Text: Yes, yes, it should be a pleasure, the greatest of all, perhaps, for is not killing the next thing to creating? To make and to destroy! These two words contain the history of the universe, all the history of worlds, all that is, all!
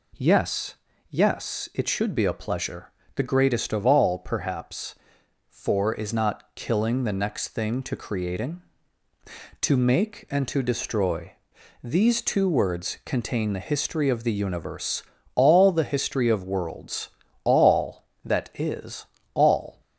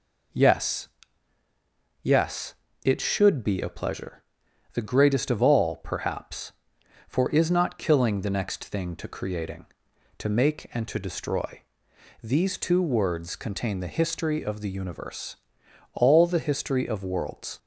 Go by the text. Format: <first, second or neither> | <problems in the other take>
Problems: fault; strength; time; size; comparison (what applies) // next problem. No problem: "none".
first | stops before "all that is all"; at 17.5 s